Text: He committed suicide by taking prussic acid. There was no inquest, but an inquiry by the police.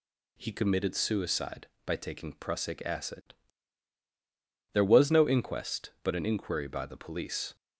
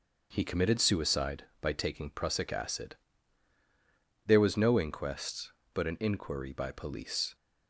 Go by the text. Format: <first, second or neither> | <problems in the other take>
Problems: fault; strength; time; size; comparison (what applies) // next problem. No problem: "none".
first | starts louder than the rest; until 1.3 s; 6.5 dB // skips "the"; at 6.7 s